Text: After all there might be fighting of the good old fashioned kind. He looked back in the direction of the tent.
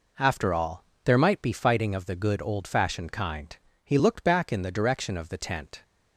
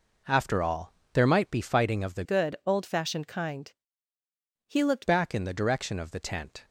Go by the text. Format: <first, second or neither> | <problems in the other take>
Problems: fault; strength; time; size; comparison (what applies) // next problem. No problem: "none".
first | pauses between "all" and "there"; slight; at 0.9 s; 0.22 s long; slight in the first // changes voice from "good" to "looked"; from 2.2 to 5.0 s; 2.8 s long